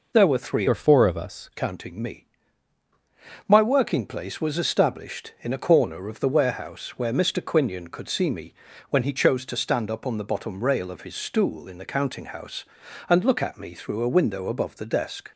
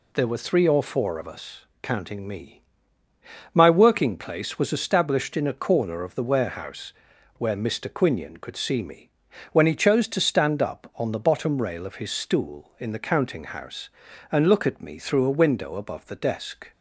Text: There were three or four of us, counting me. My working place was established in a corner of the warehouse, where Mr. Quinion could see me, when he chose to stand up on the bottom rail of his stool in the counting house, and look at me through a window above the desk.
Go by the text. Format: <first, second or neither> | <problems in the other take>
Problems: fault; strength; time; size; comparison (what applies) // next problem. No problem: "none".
second | changes voice from "or" to "us"; from 0.6 to 1.4 s; 0.8 s long